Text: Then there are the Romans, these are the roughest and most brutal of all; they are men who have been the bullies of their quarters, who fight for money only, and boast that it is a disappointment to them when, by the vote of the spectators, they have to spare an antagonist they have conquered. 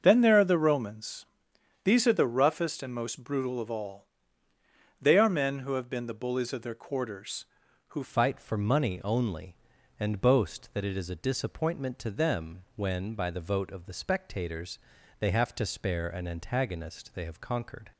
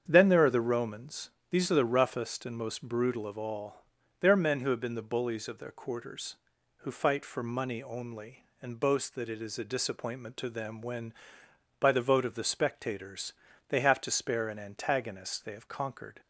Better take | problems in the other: second | starts louder than the rest; until 1.0 s; 6.5 dB; strong in the second // changes voice at "fight"; from 8.0 s on; 9.9 s long

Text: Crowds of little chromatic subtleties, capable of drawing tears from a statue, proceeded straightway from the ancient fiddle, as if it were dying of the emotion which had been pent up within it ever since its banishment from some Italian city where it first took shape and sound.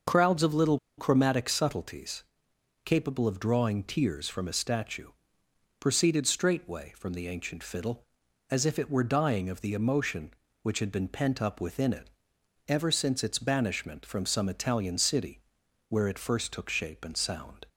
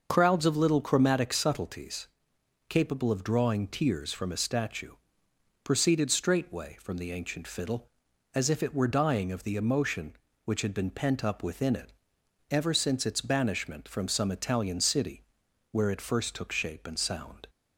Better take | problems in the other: second | pauses between "little" and "chromatic"; slight; at 0.7 s; 0.19 s long // pauses between "it" and "ever"; noticeable; at 12.0 s; 0.58 s long; noticeable in the second // pauses between "city" and "where"; noticeable; at 15.3 s; 0.48 s long; noticeable in the second

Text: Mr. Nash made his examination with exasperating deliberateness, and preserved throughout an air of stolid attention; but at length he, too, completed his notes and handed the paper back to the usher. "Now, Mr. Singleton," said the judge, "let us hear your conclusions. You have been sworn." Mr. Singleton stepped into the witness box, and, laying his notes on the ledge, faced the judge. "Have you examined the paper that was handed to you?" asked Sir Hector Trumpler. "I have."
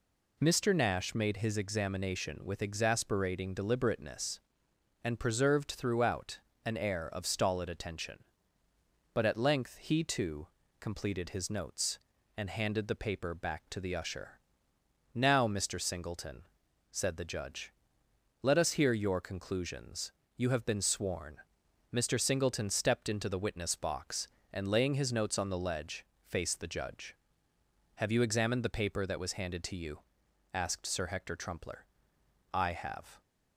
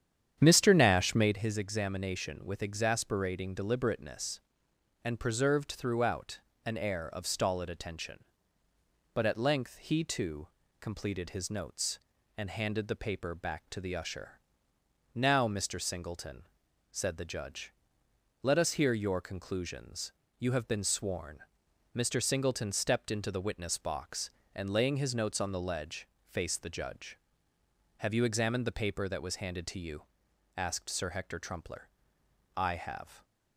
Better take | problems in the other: first | starts louder than the rest; strong; until 1.4 s; 9 dB // pauses between "throughout" and "an"; slight; at 6.3 s; 0.26 s long; slight in the first

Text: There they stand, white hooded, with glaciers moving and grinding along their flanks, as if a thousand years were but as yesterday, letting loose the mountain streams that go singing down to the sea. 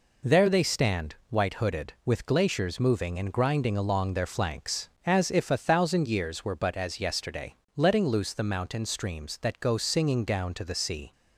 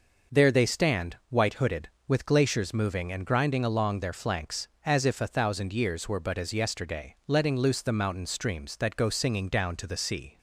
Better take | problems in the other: neither | none

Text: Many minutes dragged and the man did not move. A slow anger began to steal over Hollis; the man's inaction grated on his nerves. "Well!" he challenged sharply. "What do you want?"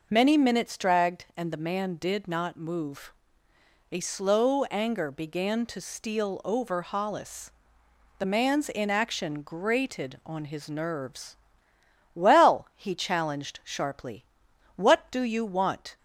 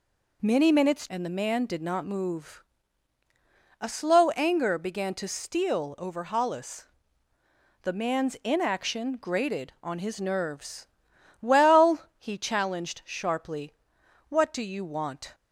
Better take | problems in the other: first | skips "dragged"; at 1.0 s

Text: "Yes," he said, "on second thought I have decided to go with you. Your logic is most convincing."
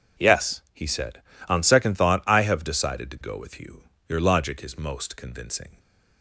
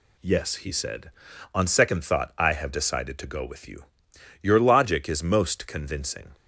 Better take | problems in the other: neither | none

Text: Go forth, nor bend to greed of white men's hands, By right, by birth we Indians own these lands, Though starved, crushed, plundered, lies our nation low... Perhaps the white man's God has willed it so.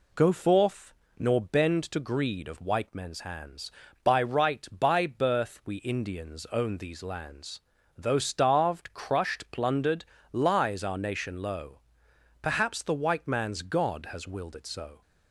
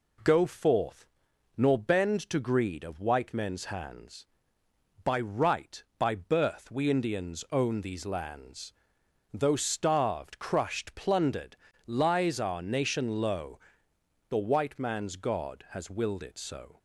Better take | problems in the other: first | skips "Perhaps"; at 13.9 s

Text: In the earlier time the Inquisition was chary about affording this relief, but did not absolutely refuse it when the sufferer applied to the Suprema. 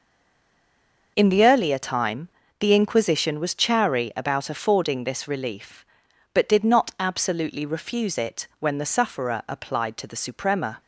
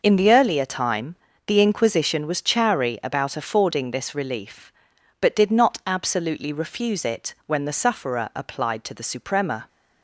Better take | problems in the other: second | stays silent before the first word; until 1.1 s; 1.1 s long // pauses between "time" and "the"; slight; at 2.2 s; 0.30 s long; slight in the second

